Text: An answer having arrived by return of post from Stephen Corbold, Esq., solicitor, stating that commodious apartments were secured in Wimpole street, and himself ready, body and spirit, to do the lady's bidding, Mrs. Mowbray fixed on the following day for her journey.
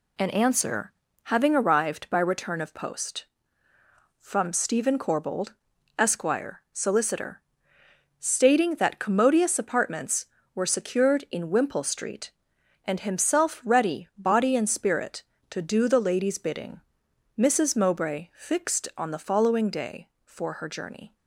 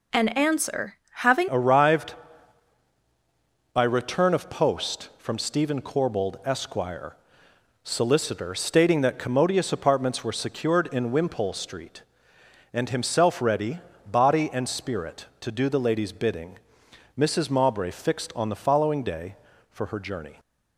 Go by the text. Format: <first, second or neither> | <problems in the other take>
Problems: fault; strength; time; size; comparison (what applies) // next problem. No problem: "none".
first | pauses between "answer" and "having"; slight; at 0.9 s; 0.22 s long; slight in the first // changes voice at "arrived"; from 1.4 s on; 18.9 s long